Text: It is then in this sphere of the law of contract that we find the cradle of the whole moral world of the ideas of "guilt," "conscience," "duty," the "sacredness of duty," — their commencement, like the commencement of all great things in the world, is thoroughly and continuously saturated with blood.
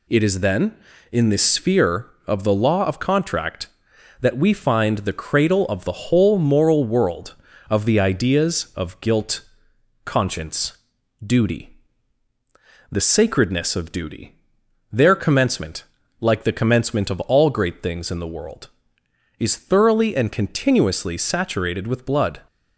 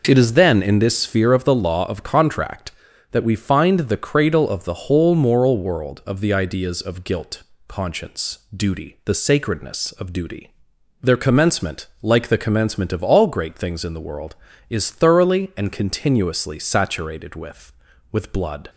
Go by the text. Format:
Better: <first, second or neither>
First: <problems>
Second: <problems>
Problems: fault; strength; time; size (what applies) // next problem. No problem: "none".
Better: first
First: none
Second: says "with" twice; at 18.1 s